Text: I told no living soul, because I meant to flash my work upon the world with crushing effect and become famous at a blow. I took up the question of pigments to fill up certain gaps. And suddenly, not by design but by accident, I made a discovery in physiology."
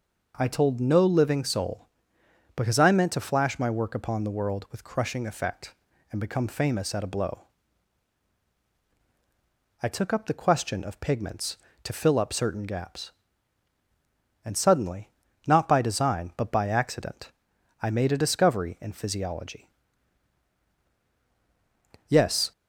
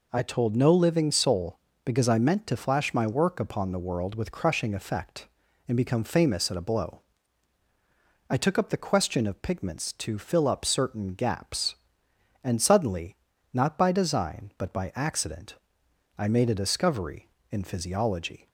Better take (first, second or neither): second